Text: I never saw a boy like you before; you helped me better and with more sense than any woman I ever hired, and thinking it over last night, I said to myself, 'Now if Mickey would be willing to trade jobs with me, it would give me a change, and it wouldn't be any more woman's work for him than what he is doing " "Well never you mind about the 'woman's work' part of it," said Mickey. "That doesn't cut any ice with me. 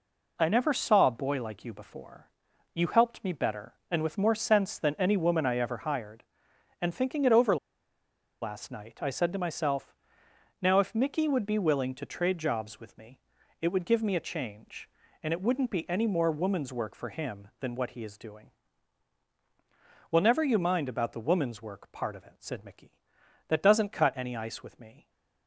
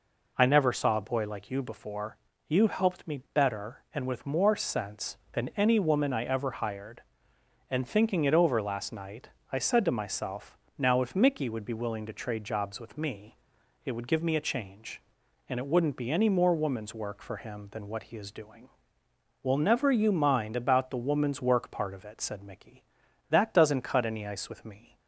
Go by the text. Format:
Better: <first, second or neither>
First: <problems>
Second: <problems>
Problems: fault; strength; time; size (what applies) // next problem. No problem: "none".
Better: second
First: pauses between "over" and "last"; noticeable; at 7.5 s; 0.85 s long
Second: none